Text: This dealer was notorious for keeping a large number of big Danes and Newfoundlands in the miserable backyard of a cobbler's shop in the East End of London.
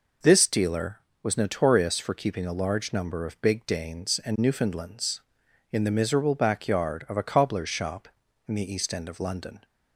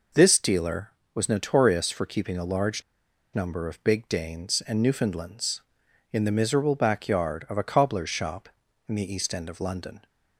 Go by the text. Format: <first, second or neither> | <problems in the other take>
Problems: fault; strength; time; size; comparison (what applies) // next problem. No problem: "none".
first | pauses between "large" and "number"; noticeable; at 2.8 s; 0.52 s long